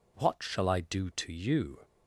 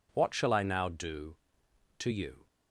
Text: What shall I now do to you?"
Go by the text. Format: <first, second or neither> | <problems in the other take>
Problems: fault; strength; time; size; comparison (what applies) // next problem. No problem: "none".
second | skips "now"; at 0.7 s